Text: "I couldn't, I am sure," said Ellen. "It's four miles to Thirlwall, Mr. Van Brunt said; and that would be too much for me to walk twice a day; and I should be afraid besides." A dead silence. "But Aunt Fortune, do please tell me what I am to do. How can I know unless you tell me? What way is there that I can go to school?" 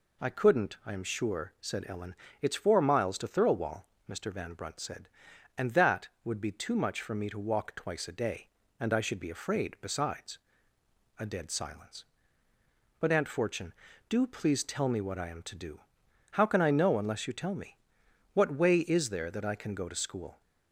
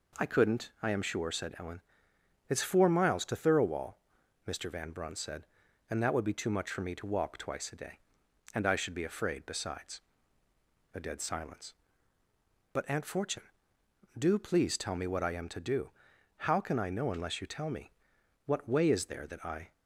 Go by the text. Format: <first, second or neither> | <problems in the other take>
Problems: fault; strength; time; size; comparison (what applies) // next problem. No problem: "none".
first | stops before "can go to school"; at 19.7 s